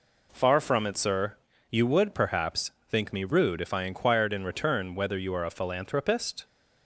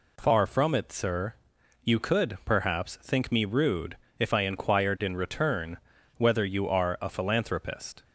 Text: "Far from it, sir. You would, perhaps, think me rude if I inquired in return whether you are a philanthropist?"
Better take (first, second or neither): first